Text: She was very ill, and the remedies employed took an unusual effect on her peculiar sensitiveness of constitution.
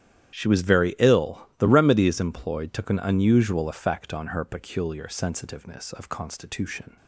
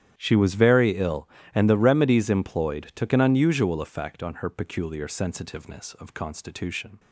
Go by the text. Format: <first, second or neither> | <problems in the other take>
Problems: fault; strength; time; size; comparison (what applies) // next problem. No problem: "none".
second | starts louder than the rest; strong; until 1.3 s; 10.5 dB; strong in the second // skips "and"; at 1.5 s